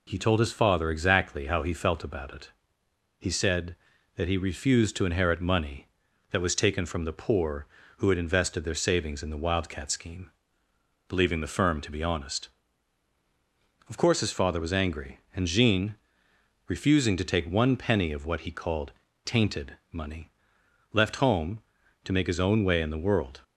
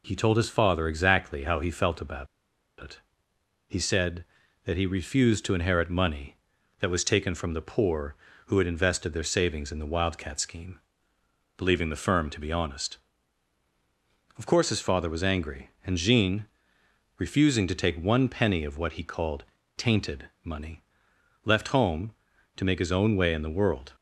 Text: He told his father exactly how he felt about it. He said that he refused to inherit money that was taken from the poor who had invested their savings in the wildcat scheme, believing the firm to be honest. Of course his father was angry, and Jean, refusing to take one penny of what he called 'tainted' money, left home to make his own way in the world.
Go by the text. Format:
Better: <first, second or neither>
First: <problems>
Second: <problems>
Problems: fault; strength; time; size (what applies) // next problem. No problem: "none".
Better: first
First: pauses between "called" and "tainted"; slight; at 18.9 s; 0.32 s long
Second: pauses between "about" and "it"; noticeable; at 2.2 s; 0.54 s long // pauses between "called" and "tainted"; slight; at 19.4 s; 0.32 s long